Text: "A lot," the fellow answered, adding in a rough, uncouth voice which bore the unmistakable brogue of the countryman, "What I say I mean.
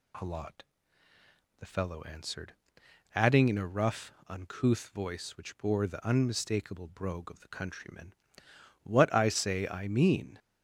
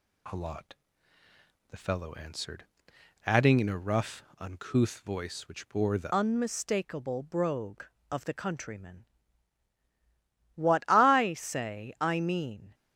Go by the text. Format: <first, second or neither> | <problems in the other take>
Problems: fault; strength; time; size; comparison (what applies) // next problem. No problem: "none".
first | changes voice at "unmistakable"; from 6.1 s on; 6.6 s long